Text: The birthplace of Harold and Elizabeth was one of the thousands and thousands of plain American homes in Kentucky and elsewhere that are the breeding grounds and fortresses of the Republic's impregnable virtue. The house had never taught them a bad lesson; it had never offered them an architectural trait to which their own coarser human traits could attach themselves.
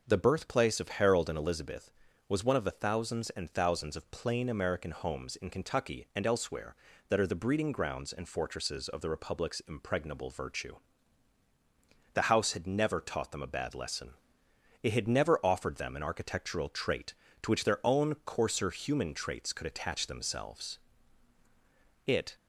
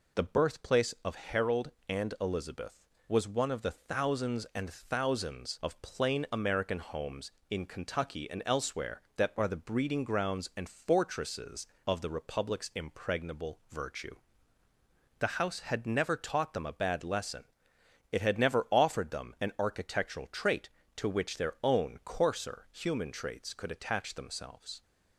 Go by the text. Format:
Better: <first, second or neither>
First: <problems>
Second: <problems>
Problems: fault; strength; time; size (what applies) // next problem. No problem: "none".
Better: second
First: goes on to say "It"; slight; from 22.0 s on; 0.30 s long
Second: none